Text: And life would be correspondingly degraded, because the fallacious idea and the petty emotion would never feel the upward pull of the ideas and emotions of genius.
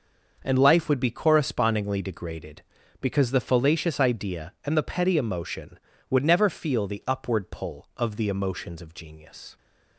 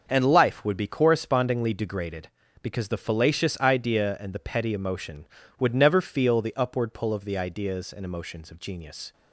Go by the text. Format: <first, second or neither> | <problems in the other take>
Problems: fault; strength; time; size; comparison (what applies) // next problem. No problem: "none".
second | skips "ideas and"; at 8.2 s